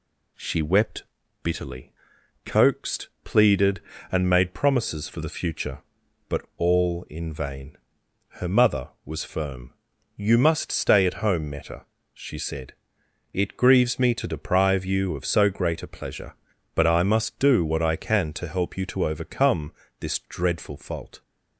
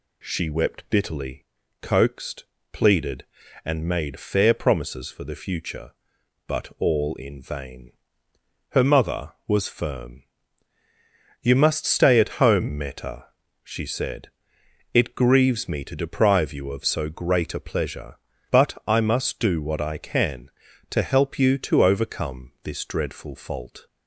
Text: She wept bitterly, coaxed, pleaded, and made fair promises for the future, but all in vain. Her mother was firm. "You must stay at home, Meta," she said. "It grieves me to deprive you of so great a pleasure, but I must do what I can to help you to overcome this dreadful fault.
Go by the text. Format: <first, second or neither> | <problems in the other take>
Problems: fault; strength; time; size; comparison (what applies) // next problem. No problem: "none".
second | pauses between "wept" and "bitterly"; at 1.0 s; 0.40 s long // skips "fair"; at 4.5 s // pauses between "overcome" and "this"; slight; at 19.7 s; 0.30 s long